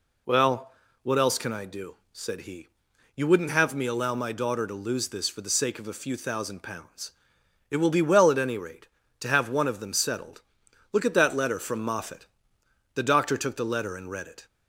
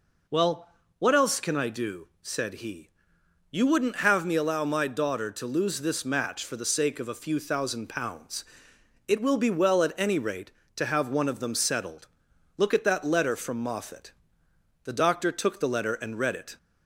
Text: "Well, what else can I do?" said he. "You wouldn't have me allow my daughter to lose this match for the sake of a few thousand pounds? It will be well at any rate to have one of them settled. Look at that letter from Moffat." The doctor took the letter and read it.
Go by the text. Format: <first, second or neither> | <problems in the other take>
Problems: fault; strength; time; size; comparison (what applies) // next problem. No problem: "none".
second | skips "match"; at 5.2 s